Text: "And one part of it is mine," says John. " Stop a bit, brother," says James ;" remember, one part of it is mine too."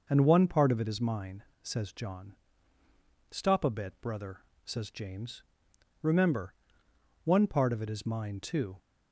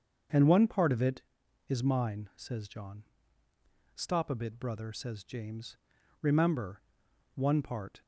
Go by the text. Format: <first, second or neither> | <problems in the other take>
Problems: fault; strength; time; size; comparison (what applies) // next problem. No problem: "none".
first | starts louder than the rest; strong; until 1.7 s; 7.5 dB; also in the first // stops before "of it is mine too"; at 8.0 s